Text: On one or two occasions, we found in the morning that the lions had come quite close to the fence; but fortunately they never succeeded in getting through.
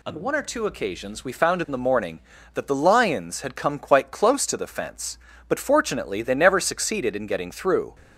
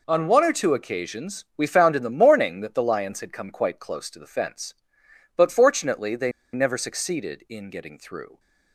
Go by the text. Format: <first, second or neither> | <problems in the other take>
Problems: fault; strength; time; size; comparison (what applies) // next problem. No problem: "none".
first | pauses between "they" and "never"; slight; at 6.2 s; 0.23 s long